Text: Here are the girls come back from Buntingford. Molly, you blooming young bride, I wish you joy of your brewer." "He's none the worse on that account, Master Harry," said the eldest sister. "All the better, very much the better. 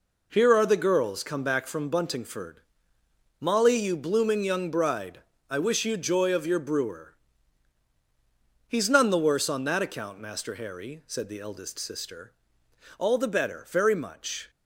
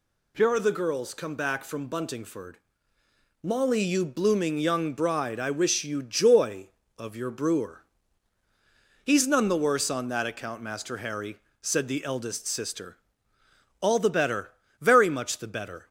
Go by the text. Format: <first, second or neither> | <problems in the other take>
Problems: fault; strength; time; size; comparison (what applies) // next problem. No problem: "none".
second | stops before "the better"; at 14.4 s